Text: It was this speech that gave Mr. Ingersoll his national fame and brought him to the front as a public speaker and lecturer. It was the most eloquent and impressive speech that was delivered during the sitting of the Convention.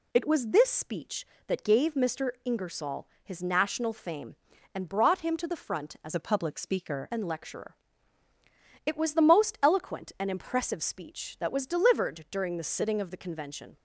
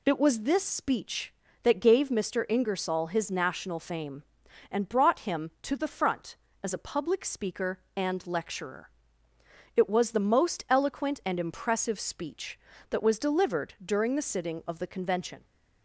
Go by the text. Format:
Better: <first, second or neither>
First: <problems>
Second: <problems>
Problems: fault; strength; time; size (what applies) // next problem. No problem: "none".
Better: second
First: pauses between "Ingersoll" and "his"; slight; at 3.0 s; 0.16 s long // changes voice from "a" to "speaker"; from 6.1 to 7.0 s; 0.9 s long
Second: none